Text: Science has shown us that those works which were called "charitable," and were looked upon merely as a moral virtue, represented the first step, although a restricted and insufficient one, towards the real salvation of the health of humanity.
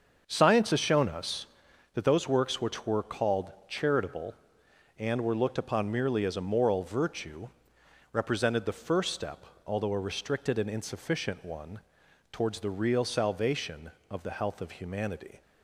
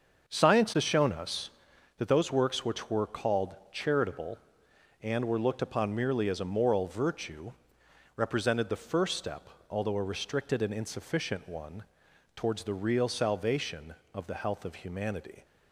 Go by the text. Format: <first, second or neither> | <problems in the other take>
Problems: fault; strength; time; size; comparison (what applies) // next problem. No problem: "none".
neither | starts louder than the rest; the same in both // pauses between "called" and "charitable"; slight; the same in both